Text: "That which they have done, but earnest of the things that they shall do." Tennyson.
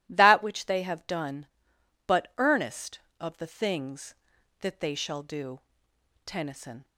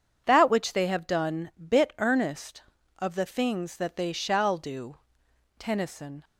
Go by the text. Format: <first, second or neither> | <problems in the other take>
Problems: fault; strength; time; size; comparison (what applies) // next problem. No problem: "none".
first | says "bit" for "but"; at 1.5 s